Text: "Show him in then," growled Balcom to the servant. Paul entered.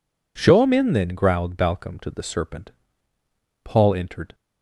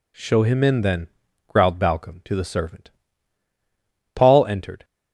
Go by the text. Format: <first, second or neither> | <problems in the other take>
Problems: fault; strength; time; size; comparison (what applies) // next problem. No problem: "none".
second | says "serpent" for "servant"; at 2.2 s